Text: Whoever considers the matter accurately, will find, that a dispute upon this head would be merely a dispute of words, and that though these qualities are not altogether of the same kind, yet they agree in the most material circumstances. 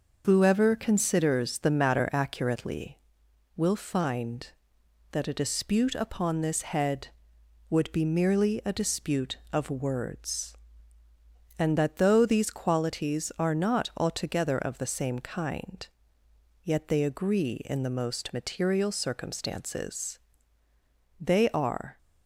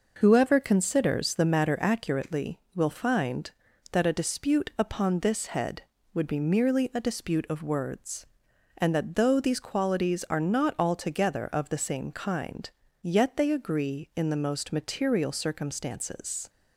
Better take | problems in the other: second | goes on to say "They are"; noticeable; from 21.1 s on; 0.78 s long

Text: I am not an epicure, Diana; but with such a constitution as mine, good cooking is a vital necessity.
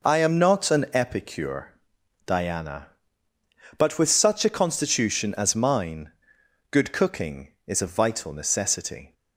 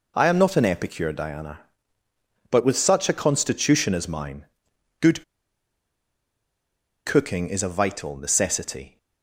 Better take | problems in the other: first | pauses between "good" and "cooking"; strong; at 5.2 s; 1.8 s long

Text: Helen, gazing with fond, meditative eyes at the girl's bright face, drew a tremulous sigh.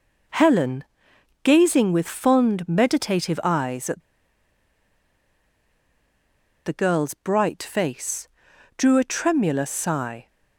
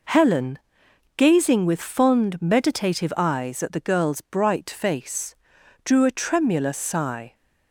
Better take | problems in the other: second | pauses between "at" and "the"; strong; at 4.0 s; 2.6 s long

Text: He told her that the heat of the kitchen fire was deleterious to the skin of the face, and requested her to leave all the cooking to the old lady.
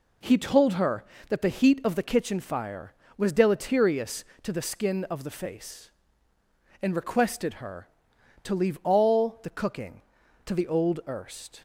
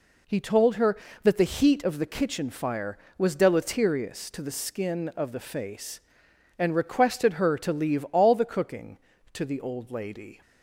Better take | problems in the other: second | says "erst" for "lady"; at 11.0 s

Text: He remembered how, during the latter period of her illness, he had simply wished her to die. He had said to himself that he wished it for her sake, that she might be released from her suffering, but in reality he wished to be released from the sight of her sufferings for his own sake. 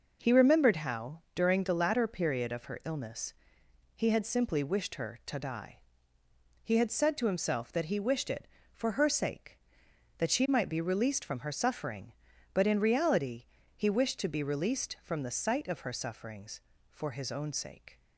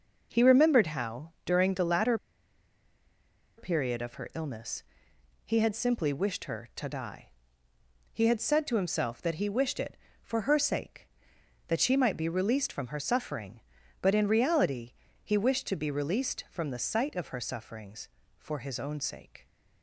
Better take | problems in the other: first | pauses between "latter" and "period"; strong; at 2.1 s; 1.4 s long // pauses between "reality" and "he"; slight; at 14.9 s; 0.28 s long; slight in the first

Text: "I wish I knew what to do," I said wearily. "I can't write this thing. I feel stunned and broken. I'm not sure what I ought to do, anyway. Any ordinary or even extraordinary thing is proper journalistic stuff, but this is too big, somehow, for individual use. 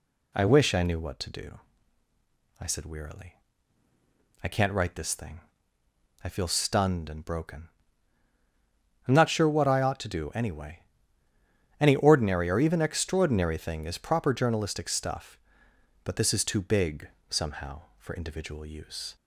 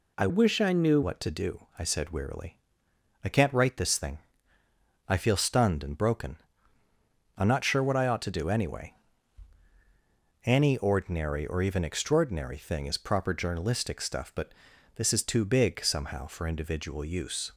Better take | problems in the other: first | changes voice from "wish" to "knew"; from 0.2 to 1.0 s; 0.8 s long // pauses between "but" and "this"; at 14.5 s; 0.44 s long

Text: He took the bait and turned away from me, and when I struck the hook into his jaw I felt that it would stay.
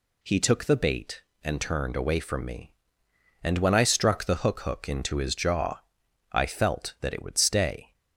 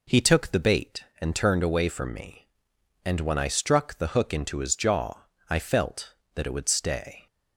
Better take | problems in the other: second | says "hook" twice; at 4.5 s // pauses between "jaw" and "I"; noticeable; at 5.7 s; 0.52 s long; slight in the second

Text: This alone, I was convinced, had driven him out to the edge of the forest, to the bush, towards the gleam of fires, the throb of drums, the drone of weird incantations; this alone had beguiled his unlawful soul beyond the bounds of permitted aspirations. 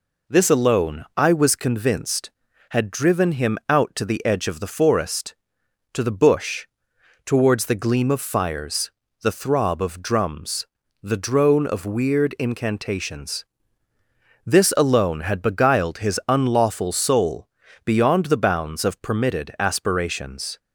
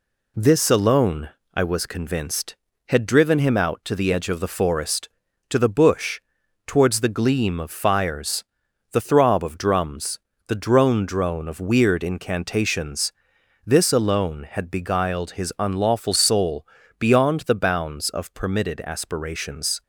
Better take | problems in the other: first | says "drone" twice; at 11.0 s // pauses between "soul" and "beyond"; slight; at 16.6 s; 0.32 s long; also in the first

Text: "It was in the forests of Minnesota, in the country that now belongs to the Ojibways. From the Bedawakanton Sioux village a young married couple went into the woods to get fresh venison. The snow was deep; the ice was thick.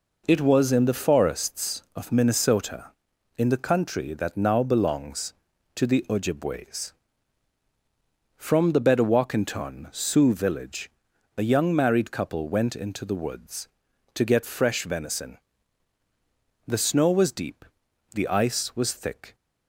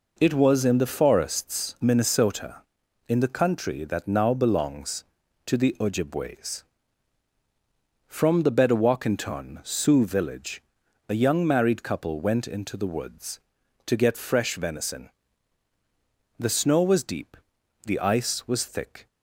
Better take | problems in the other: first | skips "of"; at 1.7 s // pauses between "village" and "a"; noticeable; at 10.6 s; 0.48 s long; noticeable in the first

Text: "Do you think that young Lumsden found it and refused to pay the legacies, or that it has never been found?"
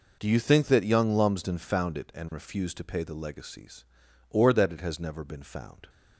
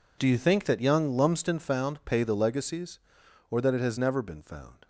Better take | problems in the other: first | skips "it and refused to"; at 2.0 s

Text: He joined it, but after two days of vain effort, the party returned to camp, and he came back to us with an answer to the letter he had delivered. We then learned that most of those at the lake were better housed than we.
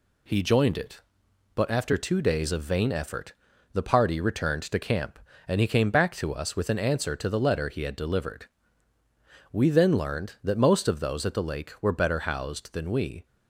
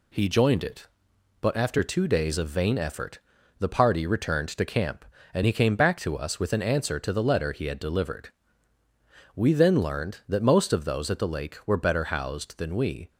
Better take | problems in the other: neither | none

